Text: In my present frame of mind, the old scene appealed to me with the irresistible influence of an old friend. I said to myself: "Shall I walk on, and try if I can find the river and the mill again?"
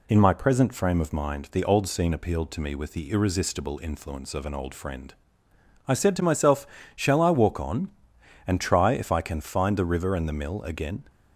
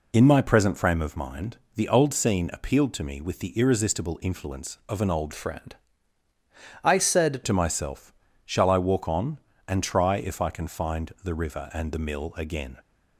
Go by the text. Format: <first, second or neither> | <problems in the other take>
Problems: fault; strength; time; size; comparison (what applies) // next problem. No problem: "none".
first | changes voice from "friend" to "said"; from 5.3 to 7.4 s; 2.1 s long